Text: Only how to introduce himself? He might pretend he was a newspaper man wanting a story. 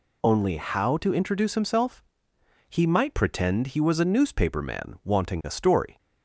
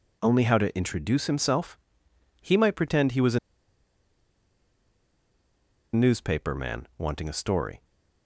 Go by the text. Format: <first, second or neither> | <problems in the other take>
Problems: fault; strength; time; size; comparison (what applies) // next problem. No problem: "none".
first | pauses between "a" and "newspaper"; strong; at 3.3 s; 2.5 s long